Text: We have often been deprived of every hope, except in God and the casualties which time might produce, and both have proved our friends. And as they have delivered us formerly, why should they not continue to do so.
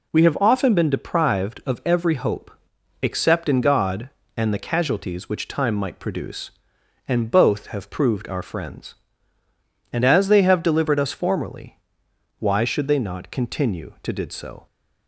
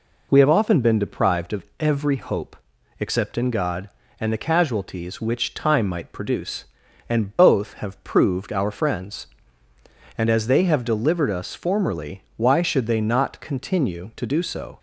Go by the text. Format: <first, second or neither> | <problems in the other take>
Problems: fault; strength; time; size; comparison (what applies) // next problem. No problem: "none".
second | says "did" for "do"; at 14.1 s